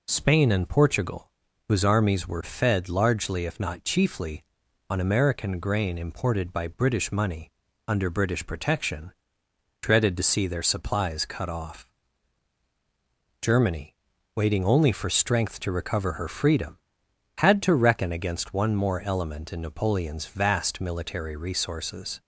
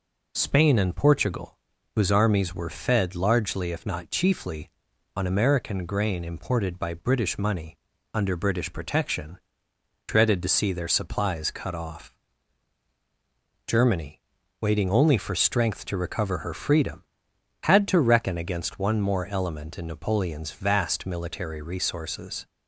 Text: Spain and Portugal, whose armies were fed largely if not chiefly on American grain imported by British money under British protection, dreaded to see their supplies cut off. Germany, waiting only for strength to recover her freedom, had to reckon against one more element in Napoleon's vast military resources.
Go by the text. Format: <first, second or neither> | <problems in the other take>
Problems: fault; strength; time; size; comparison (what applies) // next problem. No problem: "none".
neither | pauses between "money" and "under"; the same in both